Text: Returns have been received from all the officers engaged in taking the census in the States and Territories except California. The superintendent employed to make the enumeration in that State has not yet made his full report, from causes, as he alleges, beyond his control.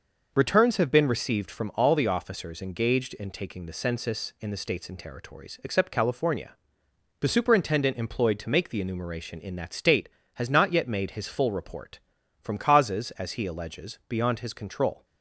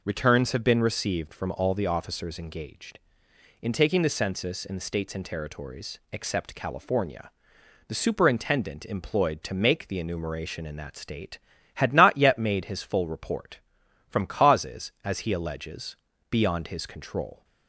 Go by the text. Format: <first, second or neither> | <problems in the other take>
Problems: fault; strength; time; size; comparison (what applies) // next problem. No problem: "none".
first | says "had" for "has"; at 11.7 s